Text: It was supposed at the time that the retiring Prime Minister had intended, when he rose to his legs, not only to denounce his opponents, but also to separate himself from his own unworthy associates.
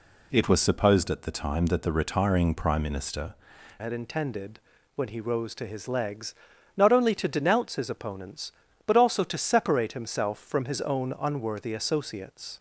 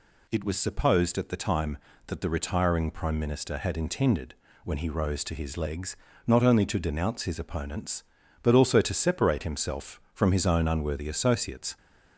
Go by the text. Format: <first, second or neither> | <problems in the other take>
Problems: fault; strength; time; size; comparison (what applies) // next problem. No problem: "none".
second | changes voice at "had"; from 3.7 s on; 8.8 s long